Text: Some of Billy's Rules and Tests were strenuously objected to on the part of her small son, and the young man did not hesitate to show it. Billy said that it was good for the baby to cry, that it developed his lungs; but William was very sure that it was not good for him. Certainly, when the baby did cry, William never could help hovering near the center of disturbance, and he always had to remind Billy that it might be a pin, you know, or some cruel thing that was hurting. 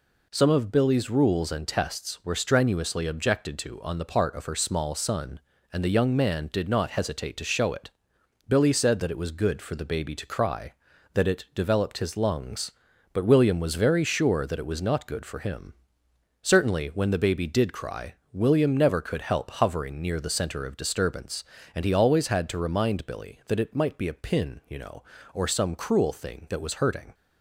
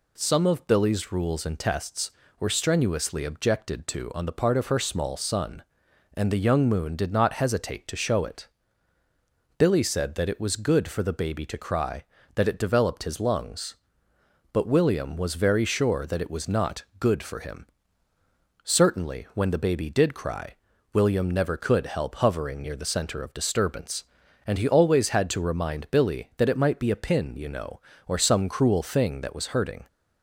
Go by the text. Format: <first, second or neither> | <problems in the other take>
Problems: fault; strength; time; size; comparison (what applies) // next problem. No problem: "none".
first | says "moon" for "man"; at 6.6 s